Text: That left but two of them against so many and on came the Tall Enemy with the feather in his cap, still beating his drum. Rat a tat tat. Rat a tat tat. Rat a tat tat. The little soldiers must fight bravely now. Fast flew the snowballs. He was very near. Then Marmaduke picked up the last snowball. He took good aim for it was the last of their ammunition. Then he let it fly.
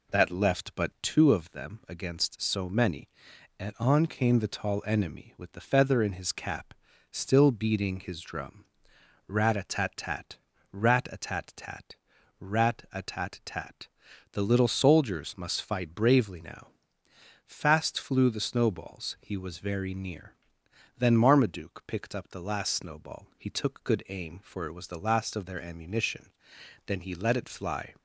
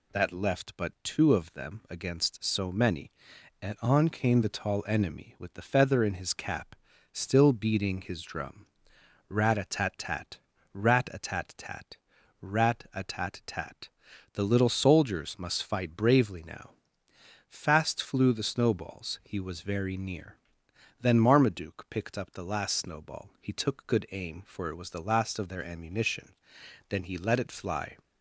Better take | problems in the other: second | starts louder than the rest; until 1.3 s; 3.5 dB

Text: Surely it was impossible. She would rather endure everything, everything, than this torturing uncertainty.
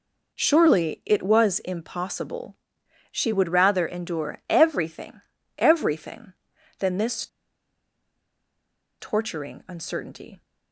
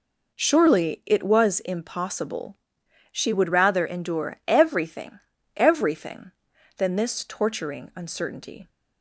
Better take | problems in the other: second | pauses between "this" and "torturing"; strong; at 7.2 s; 1.7 s long

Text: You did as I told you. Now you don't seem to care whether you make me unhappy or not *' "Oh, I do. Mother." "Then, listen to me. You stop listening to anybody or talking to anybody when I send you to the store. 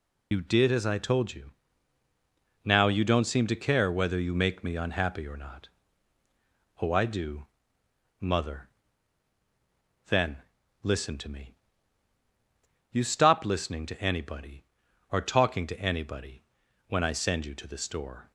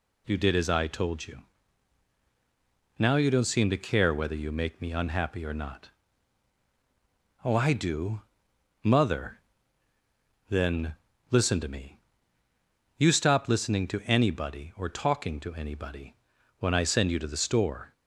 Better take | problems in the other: second | loses the start of "You"; at 0.3 s; 45 ms // pauses between "anybody" and "when"; at 16.4 s; 0.44 s long; also in the second

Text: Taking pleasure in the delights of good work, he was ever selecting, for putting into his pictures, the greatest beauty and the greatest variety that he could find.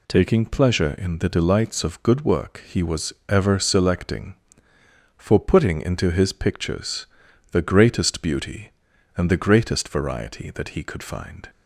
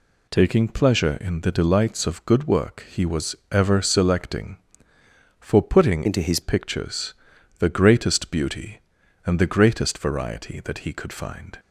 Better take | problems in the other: first | pauses between "was" and "ever"; slight; at 3.3 s; 0.16 s long; slight in the first // changes voice from "into" to "his"; from 6.0 to 6.3 s; 0.3 s long

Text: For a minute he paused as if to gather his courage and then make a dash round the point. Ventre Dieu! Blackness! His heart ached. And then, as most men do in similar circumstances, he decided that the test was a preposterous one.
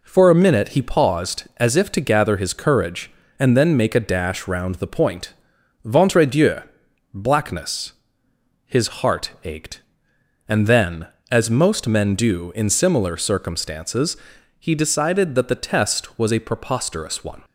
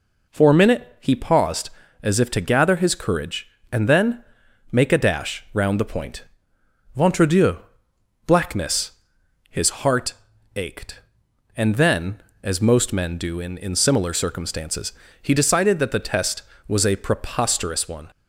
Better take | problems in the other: first | pauses between "then" and "make"; noticeable; at 4.2 s; 0.48 s long // pauses between "heart" and "ached"; at 10.1 s; 0.42 s long // says "in" twice; at 13.5 s

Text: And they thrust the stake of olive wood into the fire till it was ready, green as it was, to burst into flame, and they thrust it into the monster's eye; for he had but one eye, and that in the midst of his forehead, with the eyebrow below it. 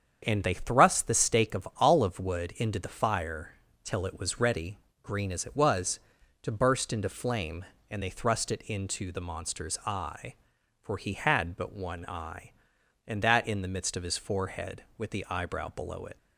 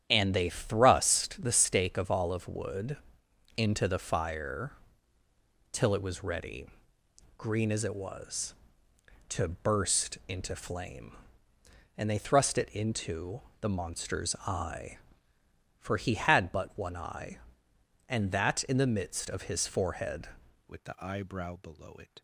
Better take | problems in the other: first | starts louder than the rest; strong; until 1.1 s; 9.5 dB; strong in the first // pauses between "wood" and "into"; noticeable; at 2.9 s; 0.60 s long // pauses between "fire" and "till"; at 4.7 s; 1.0 s long; slight in the first // pauses between "into" and "the"; slight; at 13.3 s; 0.22 s long // changes voice at "with"; from 20.6 s on; 1.6 s long

